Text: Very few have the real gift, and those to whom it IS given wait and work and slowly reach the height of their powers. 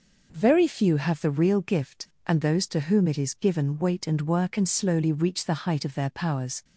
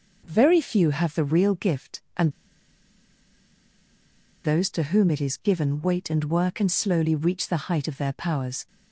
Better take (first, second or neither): first